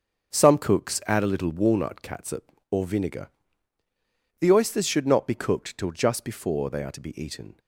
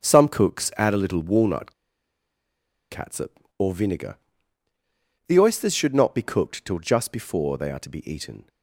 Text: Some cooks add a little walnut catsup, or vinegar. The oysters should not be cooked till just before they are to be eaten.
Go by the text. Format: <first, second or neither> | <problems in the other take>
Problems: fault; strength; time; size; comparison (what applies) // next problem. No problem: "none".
first | starts louder than the rest; until 1.1 s; 6.5 dB; also in the first // pauses between "walnut" and "catsup"; at 1.7 s; 1.1 s long